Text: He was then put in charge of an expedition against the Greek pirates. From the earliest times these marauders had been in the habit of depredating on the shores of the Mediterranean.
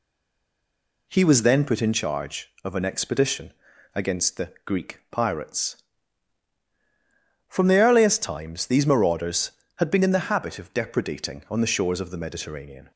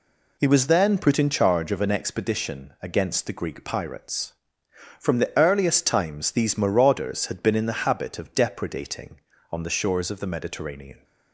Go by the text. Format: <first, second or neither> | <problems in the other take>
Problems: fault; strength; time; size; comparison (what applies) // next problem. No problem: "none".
second | stays silent before the first word; until 1.0 s; 1.0 s long // pauses between "expedition" and "against"; at 3.5 s; 0.44 s long